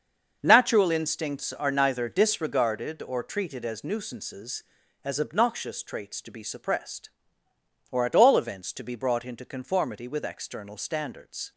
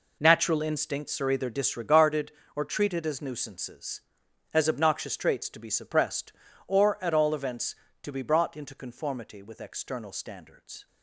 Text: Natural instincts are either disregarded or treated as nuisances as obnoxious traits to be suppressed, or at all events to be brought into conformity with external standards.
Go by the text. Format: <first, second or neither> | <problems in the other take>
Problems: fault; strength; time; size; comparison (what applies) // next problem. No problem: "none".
second | starts louder than the rest; until 1.4 s; 6.5 dB // says "neither" for "either"; at 1.7 s